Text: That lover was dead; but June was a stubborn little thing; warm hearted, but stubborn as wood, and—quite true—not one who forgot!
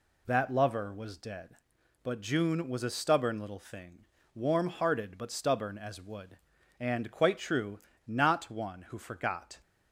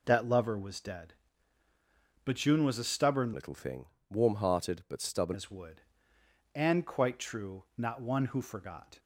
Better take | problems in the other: first | changes voice from "little" to "stubborn"; from 3.3 to 5.3 s; 2.0 s long

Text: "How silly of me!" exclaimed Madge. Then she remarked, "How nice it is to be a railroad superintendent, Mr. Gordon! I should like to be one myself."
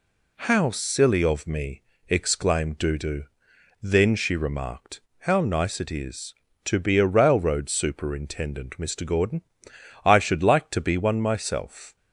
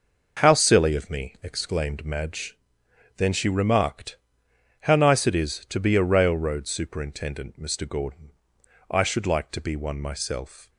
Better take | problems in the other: second | says "Dudu" for "Madge"; at 2.7 s

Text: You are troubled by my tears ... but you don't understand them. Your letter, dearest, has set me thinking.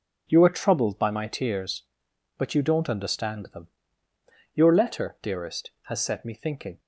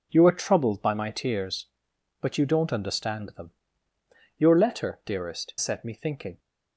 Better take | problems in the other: first | skips "has"; at 5.5 s

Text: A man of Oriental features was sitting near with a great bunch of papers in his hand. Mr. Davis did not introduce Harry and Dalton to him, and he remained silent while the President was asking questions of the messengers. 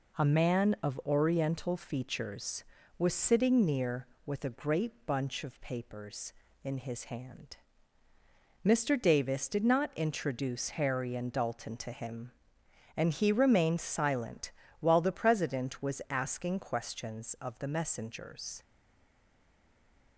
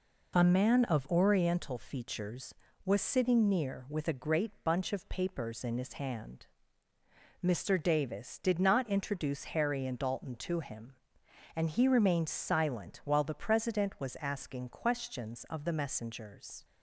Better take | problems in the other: second | pauses between "great" and "bunch"; slight; at 4.9 s; 0.16 s long // pauses between "silent" and "while"; slight; at 14.5 s; 0.28 s long // stays silent after the last word; noticeable; from 18.6 s on; 1.5 s long

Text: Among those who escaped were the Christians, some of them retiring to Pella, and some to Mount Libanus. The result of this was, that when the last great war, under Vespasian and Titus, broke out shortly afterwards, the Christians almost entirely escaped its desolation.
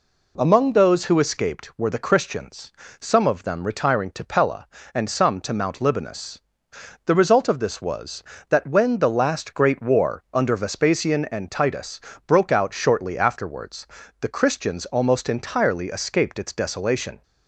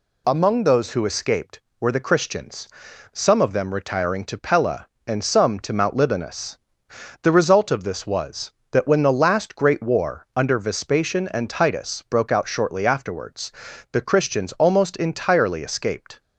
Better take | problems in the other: first | stops before "its desolation"; at 16.2 s

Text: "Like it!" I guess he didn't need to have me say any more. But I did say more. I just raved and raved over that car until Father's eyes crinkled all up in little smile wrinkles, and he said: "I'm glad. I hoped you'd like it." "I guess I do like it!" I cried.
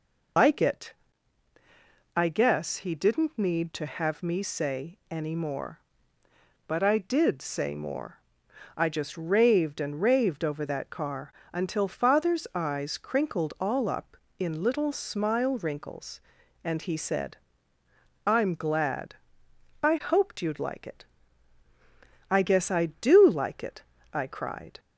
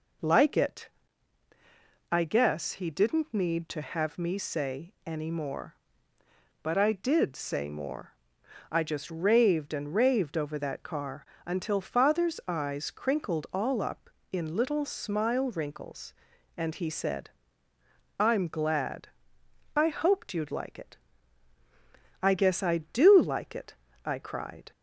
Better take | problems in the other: second | loses the start of "Like"; at 0.3 s; 100 ms // pauses between "car" and "until"; slight; at 11.3 s; 0.20 s long; slight in the second

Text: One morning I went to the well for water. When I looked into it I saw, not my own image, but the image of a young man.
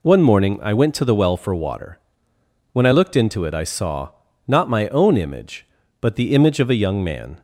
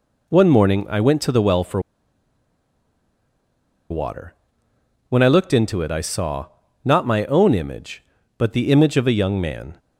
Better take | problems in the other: first | pauses between "for" and "water"; strong; at 1.7 s; 2.1 s long

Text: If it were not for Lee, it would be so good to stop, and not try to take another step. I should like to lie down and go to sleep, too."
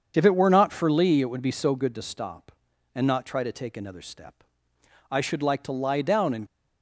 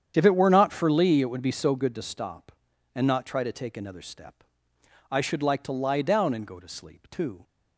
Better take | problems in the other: second | starts louder than the rest; until 1.1 s; 7 dB; strong in the second // stops before "go to sleep too"; at 6.4 s

